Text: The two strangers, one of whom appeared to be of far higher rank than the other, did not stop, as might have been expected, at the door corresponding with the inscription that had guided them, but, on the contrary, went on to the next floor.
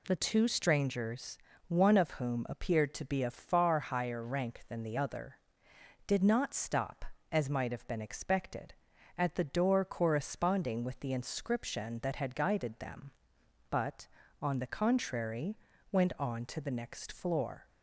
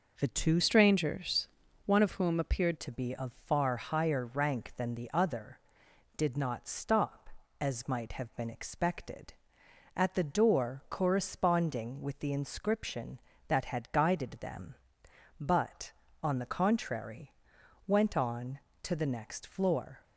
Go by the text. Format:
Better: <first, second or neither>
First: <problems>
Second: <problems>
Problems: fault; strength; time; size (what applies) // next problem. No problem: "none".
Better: first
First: none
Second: changes voice from "strangers" to "appeared"; from 0.6 to 2.7 s; 2.1 s long